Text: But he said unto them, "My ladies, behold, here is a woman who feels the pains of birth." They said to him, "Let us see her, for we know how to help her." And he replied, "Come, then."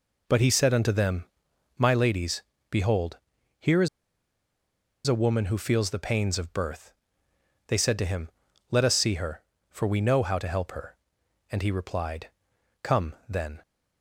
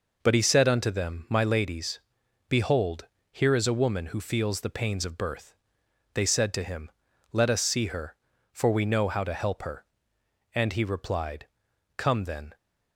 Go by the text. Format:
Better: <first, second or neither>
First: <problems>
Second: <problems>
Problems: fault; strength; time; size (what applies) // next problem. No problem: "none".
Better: second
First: pauses between "is" and "a"; at 3.8 s; 1.1 s long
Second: none